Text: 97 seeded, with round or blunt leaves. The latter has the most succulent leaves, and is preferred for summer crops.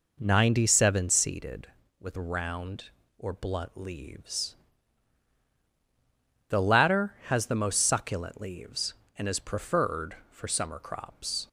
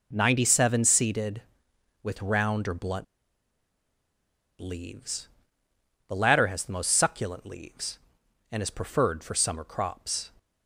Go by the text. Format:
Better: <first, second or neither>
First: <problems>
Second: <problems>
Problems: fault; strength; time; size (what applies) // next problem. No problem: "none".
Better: first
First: none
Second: pauses between "blunt" and "leaves"; strong; at 3.0 s; 1.5 s long